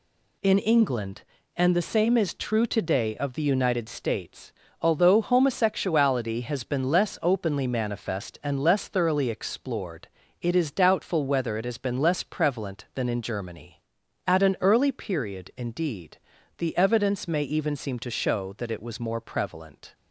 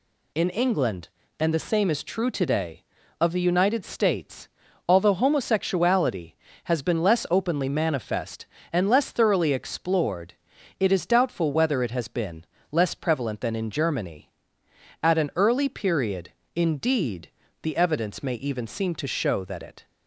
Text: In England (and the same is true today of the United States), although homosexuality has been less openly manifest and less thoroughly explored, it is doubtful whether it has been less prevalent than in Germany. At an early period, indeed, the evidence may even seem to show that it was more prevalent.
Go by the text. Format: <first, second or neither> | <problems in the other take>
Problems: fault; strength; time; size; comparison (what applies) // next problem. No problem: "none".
first | pauses between "been" and "less"; slight; at 12.4 s; 0.26 s long // stops before "was more prevalent"; at 19.8 s